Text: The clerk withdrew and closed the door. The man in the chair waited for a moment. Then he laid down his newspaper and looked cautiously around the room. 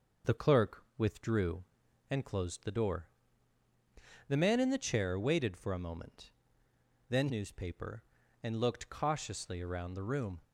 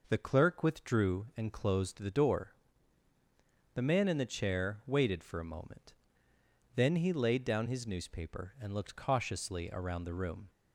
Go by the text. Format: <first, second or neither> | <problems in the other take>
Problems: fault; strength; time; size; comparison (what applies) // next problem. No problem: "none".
second | pauses between "clerk" and "withdrew"; slight; at 0.8 s; 0.16 s long // skips "he laid down his"; at 7.2 s